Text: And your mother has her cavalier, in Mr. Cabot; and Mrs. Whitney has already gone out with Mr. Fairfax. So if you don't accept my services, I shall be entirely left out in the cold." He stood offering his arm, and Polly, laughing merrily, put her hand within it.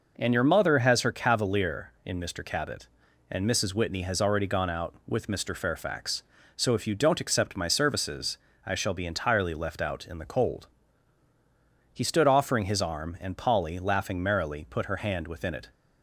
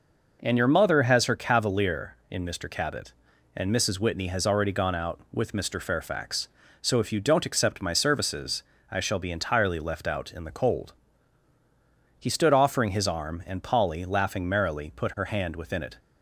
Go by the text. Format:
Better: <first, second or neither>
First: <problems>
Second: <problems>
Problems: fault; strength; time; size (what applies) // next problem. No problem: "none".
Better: neither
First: none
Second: none